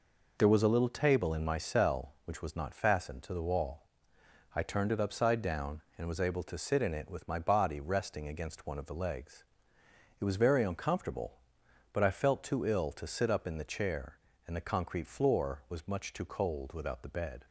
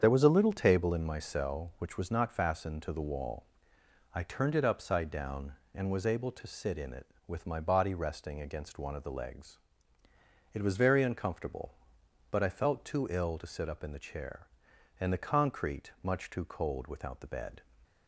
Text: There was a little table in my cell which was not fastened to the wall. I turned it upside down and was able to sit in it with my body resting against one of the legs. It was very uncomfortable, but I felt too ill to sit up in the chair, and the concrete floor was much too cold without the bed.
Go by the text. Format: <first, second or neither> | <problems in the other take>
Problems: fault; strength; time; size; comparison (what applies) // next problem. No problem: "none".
first | starts louder than the rest; strong; until 1.0 s; 7.5 dB // skips "floor was"; at 15.9 s